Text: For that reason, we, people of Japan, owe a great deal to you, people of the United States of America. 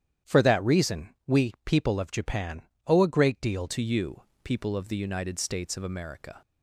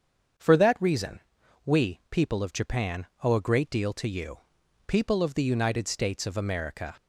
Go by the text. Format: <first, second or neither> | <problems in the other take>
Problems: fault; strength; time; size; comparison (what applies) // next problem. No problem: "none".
second | starts louder than the rest; strong; until 1.4 s; 10 dB; strong in the second // changes voice at "to"; from 3.6 s on; 2.8 s long